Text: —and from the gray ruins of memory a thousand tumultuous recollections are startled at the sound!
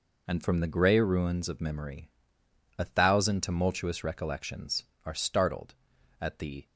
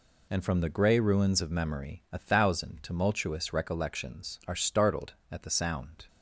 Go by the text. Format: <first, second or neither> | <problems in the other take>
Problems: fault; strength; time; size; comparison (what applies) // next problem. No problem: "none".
second | pauses between "memory" and "a"; noticeable; at 2.0 s; 0.70 s long // stops before "sound"; at 6.6 s